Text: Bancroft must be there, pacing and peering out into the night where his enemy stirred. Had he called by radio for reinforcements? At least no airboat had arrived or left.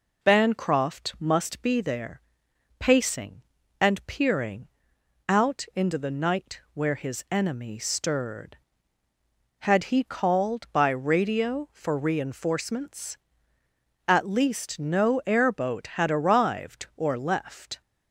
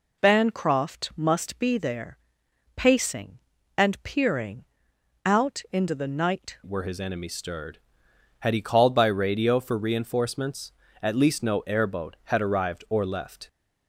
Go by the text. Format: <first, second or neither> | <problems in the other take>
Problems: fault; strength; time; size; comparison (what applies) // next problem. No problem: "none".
first | pauses between "peering" and "out"; noticeable; at 4.6 s; 0.60 s long; noticeable in the first // changes voice at "where"; from 6.6 s on; 6.8 s long